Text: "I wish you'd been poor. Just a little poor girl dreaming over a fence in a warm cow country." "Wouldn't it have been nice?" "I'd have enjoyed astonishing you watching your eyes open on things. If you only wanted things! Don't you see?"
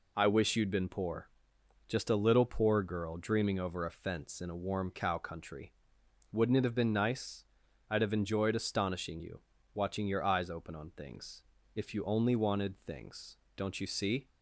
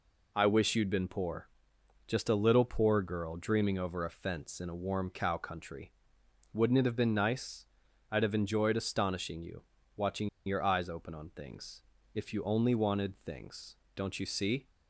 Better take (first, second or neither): first